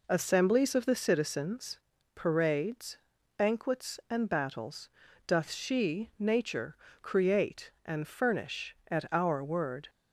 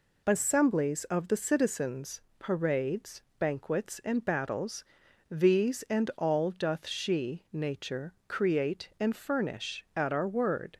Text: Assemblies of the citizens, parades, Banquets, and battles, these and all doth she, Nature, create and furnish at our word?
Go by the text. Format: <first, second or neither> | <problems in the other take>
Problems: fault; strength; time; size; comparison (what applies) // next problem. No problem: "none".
second | skips "these and all"; at 5.0 s